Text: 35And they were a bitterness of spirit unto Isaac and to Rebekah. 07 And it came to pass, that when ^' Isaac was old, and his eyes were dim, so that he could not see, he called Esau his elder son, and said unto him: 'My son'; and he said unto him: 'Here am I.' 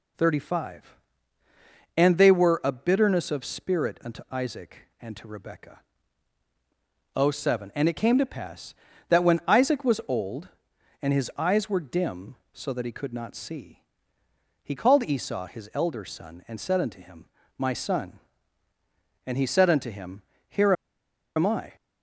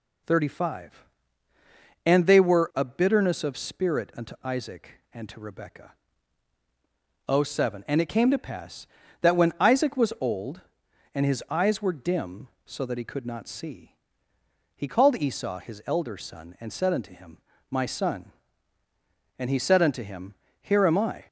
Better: second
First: pauses between "Here" and "am"; noticeable; at 20.7 s; 0.63 s long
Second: none

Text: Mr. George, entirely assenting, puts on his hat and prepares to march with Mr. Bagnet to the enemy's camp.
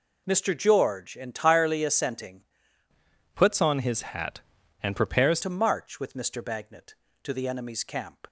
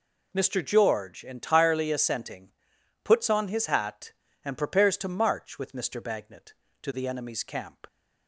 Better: second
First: changes voice from "puts" to "prepares"; from 3.3 to 5.4 s; 2.1 s long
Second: none

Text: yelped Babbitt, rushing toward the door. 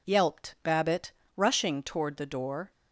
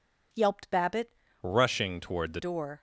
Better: first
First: none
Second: changes voice from "rushing" to "the"; from 1.4 to 2.3 s; 0.9 s long

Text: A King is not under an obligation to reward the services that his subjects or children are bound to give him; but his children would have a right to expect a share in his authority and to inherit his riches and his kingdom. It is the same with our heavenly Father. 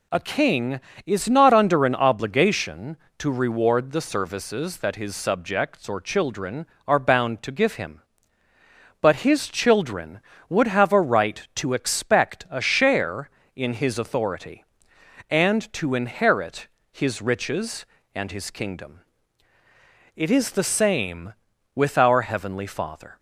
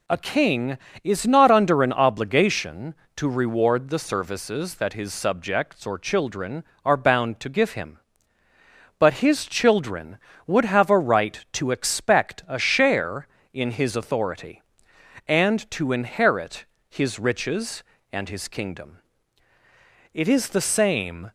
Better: first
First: pauses between "inherit" and "his"; slight; at 16.6 s; 0.22 s long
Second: pauses between "inherit" and "his"; slight; at 16.6 s; 0.22 s long // stops before "with our heavenly Father"; at 21.2 s

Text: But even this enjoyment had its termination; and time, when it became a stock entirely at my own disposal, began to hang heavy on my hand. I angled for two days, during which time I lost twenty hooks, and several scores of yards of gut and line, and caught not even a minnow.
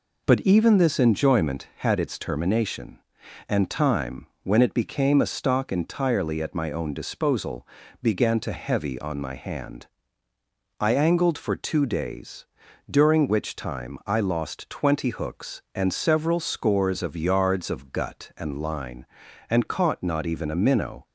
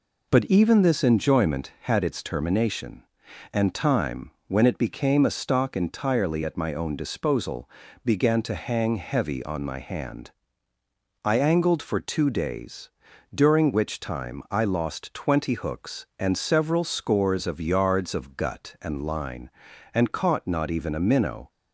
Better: second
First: skips "hang"; at 8.5 s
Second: none

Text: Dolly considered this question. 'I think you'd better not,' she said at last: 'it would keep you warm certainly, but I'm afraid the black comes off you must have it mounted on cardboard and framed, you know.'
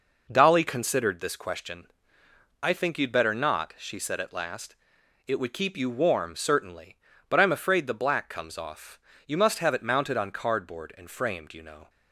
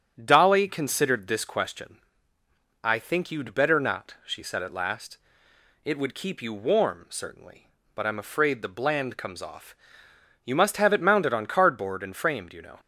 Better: first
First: pauses between "off" and "you"; slight; at 8.9 s; 0.30 s long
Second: starts louder than the rest; strong; until 1.2 s; 7.5 dB // says "bland" for "black"; at 8.6 s // pauses between "off" and "you"; noticeable; at 9.7 s; 0.70 s long

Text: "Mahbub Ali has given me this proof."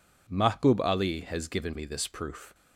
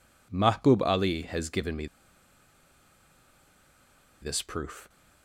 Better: first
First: none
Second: pauses between "me" and "this"; strong; at 1.8 s; 2.3 s long

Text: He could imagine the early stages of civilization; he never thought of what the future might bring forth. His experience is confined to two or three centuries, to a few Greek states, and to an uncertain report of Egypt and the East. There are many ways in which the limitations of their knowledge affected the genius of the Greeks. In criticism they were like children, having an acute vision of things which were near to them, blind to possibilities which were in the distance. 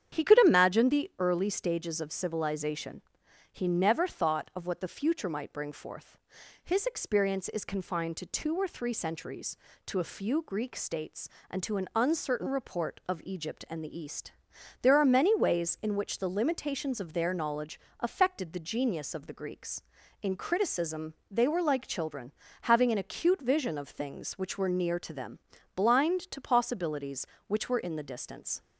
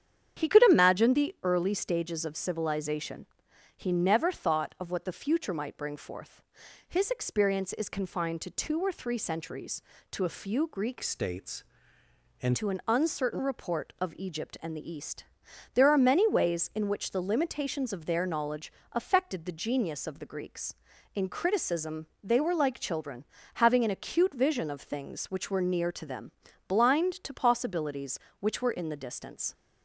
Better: first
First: starts louder than the rest; strong; until 1.2 s; 9 dB // pauses between "knowledge" and "affected"; slight; at 17.8 s; 0.20 s long // pauses between "criticism" and "they"; slight; at 21.1 s; 0.16 s long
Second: starts louder than the rest; strong; until 1.4 s; 9 dB // changes voice from "states" to "and"; from 11.0 to 12.5 s; 1.5 s long // pauses between "knowledge" and "affected"; slight; at 18.7 s; 0.20 s long // pauses between "criticism" and "they"; slight; at 22.0 s; 0.16 s long

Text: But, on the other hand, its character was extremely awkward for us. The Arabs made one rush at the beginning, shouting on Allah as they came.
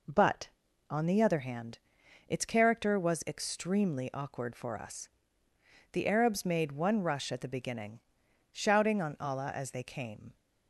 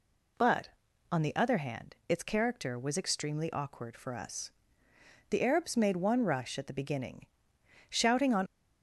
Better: first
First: none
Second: stops before "Allah as they came"; at 8.4 s

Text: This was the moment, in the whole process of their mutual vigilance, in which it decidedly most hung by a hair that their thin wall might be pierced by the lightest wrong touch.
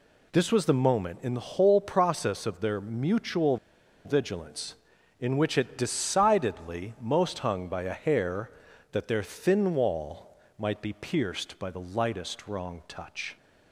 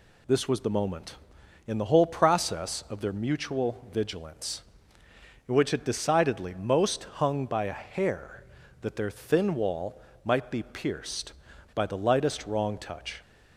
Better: second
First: pauses between "mutual" and "vigilance"; noticeable; at 3.5 s; 0.49 s long // pauses between "wall" and "might"; slight; at 10.3 s; 0.22 s long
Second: pauses between "wall" and "might"; slight; at 10.0 s; 0.24 s long

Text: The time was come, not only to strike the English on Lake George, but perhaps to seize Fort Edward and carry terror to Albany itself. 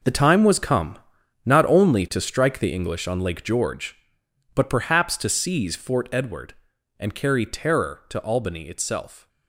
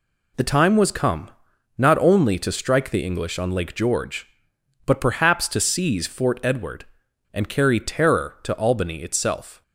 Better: second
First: gets quieter; strong; throughout; 12.5 dB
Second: none

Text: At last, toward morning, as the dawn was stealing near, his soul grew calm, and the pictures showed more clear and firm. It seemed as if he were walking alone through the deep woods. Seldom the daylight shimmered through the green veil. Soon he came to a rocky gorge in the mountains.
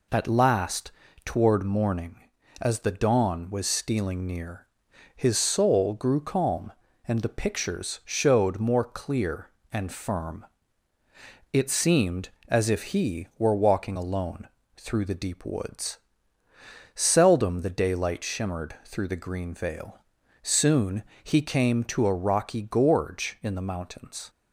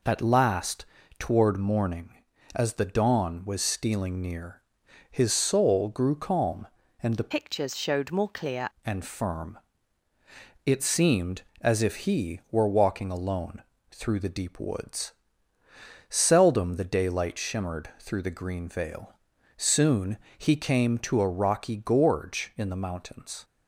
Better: first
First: pauses between "alone" and "through"; slight; at 14.4 s; 0.28 s long // pauses between "Soon" and "he"; slight; at 21.0 s; 0.22 s long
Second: changes voice from "pictures" to "clear"; from 7.3 to 8.6 s; 1.3 s long // pauses between "alone" and "through"; slight; at 13.6 s; 0.28 s long // pauses between "Soon" and "he"; slight; at 20.1 s; 0.22 s long

